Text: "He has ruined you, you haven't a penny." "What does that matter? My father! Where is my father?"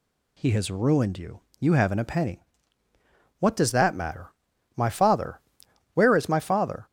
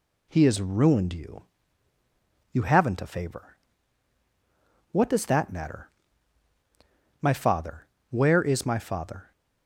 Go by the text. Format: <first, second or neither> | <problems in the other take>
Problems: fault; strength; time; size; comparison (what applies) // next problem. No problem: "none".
first | says "favor" for "penny"; at 3.0 s